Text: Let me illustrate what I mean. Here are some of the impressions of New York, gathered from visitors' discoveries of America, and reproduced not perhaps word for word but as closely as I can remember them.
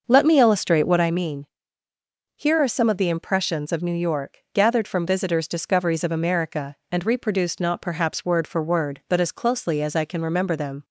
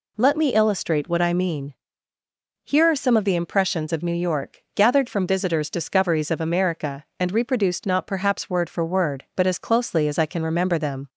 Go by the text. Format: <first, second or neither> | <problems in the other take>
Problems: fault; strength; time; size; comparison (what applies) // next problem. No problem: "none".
second | starts louder than the rest; noticeable; until 1.1 s; 6 dB